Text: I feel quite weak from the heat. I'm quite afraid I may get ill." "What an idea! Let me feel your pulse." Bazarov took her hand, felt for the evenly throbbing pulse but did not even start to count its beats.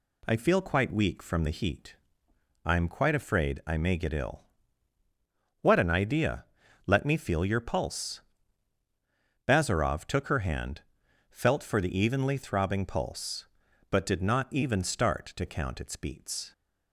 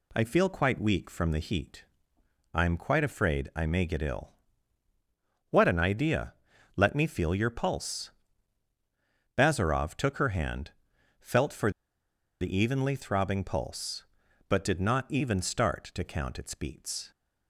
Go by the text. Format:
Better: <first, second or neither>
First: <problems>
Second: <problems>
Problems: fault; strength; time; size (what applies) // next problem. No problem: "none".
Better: first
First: none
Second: pauses between "for" and "the"; noticeable; at 11.6 s; 0.70 s long